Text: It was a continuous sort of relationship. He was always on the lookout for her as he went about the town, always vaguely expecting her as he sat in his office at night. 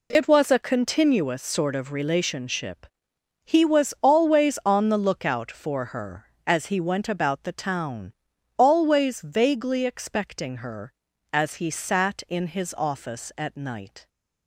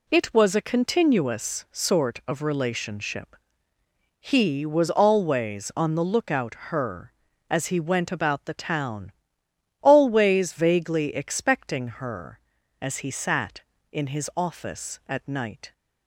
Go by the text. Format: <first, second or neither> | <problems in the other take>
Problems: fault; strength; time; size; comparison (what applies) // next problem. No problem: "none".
first | skips "for"; at 6.6 s